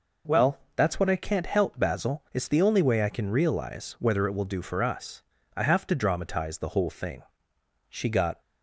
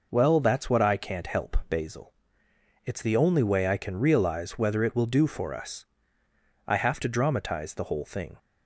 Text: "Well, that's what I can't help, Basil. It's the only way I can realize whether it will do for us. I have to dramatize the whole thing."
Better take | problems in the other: second | goes on to say "She got"; from 7.8 s on; 0.52 s long

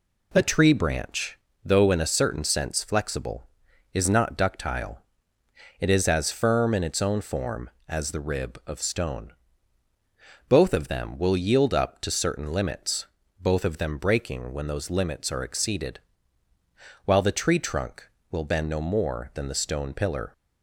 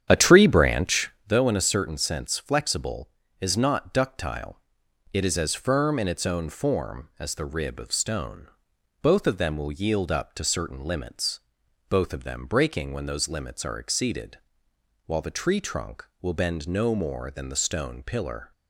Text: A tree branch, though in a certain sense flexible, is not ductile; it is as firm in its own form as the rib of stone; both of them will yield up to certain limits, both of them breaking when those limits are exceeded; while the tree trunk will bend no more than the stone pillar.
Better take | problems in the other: first | starts louder than the rest; strong; until 1.4 s; 9 dB

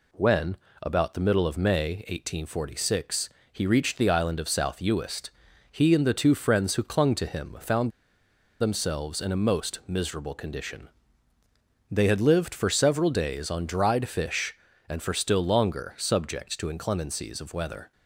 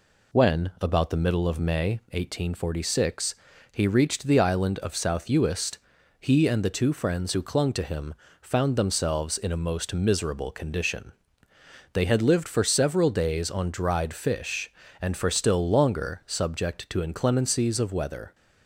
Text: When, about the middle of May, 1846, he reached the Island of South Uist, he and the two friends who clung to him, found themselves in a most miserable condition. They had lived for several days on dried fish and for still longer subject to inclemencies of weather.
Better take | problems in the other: second | pauses between "found" and "themselves"; noticeable; at 7.8 s; 0.70 s long

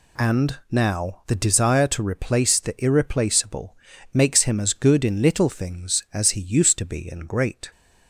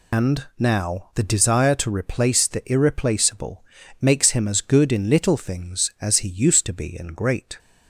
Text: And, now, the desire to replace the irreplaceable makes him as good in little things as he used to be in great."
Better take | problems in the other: first | loses the start of "And"; at 0.1 s; 95 ms // pauses between "irreplaceable" and "makes"; slight; at 3.6 s; 0.36 s long; slight in the first

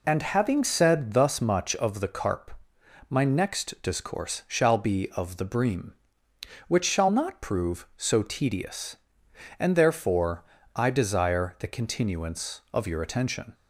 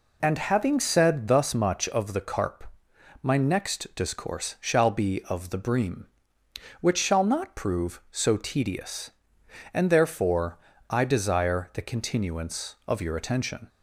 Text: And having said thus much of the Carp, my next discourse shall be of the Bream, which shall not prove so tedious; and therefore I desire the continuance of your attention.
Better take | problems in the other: neither | pauses between "therefore" and "I"; slight; the same in both

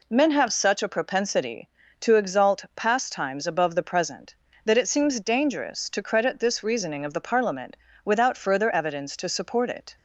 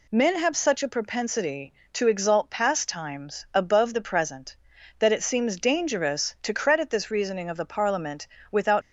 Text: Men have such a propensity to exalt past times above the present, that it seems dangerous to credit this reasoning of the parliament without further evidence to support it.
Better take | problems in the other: first | pauses between "parliament" and "without"; slight; at 8.2 s; 0.28 s long; slight in the first // stops before "further evidence to support it"; at 8.8 s

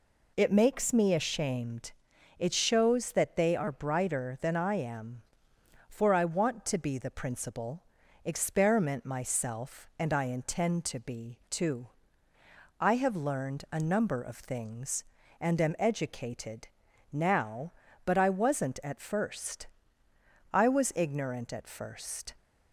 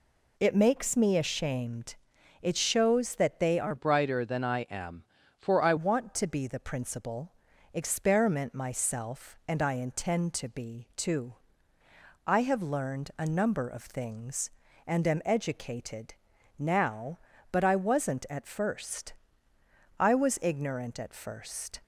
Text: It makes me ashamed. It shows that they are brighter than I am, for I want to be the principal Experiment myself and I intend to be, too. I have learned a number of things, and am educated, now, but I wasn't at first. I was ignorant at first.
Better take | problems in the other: first | changes voice from "brighter" to "I"; from 3.7 to 5.7 s; 2.0 s long // pauses between "principal" and "Experiment"; at 7.3 s; 0.42 s long; also in the first

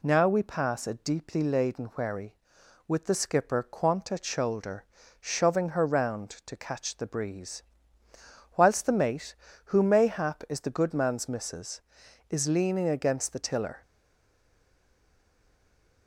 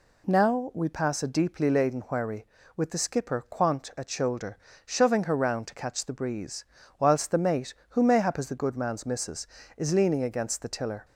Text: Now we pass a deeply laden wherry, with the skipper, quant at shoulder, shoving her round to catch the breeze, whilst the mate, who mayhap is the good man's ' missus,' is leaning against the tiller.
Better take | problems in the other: second | stays silent after the last word; from 13.8 s on; 2.2 s long

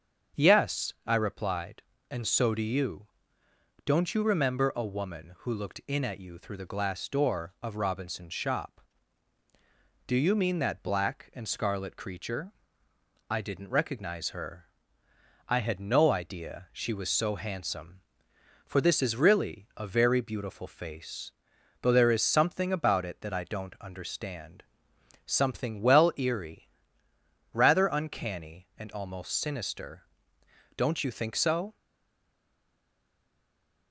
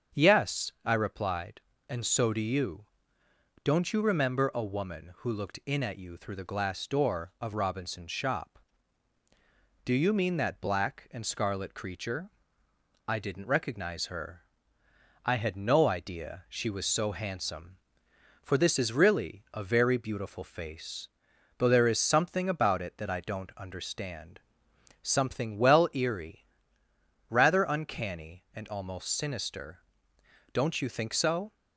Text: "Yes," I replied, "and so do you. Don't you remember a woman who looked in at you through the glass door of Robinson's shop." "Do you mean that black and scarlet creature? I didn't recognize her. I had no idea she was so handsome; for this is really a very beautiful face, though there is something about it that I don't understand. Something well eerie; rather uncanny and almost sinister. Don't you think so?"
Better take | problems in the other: second | starts louder than the rest; until 1.4 s; 7 dB; also in the second // stays silent after the last word; from 31.7 s on; 2.2 s long

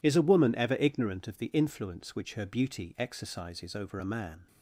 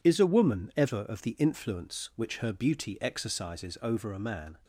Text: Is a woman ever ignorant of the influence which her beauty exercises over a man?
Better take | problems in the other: first | skips "ignorant"; at 1.0 s

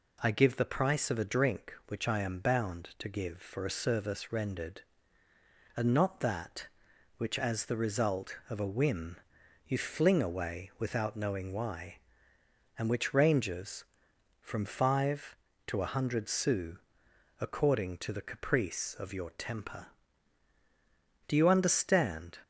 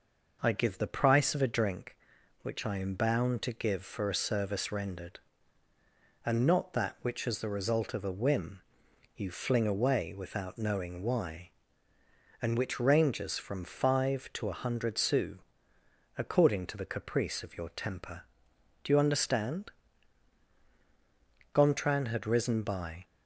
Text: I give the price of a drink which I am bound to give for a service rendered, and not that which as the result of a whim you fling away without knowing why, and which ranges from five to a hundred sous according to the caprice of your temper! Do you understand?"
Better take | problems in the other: first | pauses between "whim" and "you"; noticeable; at 8.6 s; 0.56 s long; noticeable in the first // pauses between "sous" and "according"; noticeable; at 15.3 s; 0.78 s long; noticeable in the first // goes on to say "Gontran had risen by"; from 21.5 s on; 1.5 s long

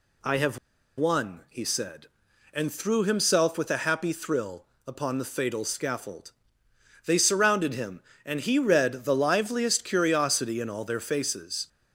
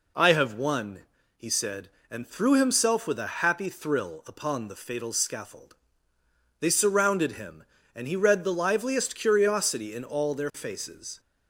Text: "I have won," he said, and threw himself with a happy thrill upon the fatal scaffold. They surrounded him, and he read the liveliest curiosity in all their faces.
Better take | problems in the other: second | pauses between "have" and "won"; at 0.5 s; 0.39 s long // pauses between "thrill" and "upon"; slight; at 4.6 s; 0.20 s long

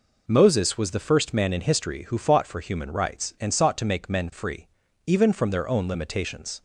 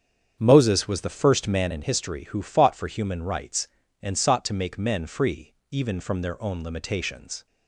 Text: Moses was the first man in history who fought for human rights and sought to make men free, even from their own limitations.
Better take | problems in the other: first | starts louder than the rest; strong; until 1.8 s; 8 dB

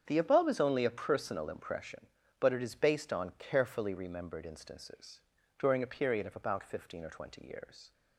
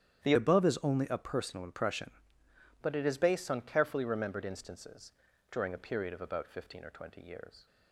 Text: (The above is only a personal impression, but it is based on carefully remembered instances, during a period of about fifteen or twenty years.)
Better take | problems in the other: first | starts louder than the rest; strong; until 1.2 s; 9.5 dB; strong in the first // changes voice from "above" to "impression"; from 0.3 to 2.1 s; 1.8 s long

